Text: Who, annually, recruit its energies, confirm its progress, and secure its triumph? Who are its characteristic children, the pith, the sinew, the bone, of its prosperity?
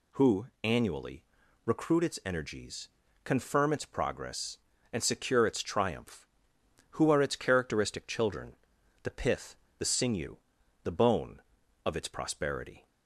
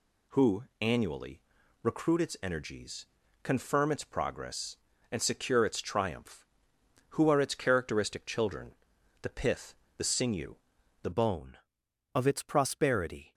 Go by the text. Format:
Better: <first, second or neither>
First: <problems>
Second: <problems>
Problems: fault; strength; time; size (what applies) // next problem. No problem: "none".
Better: first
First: none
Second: changes voice at "bone"; from 11.1 s on; 2.2 s long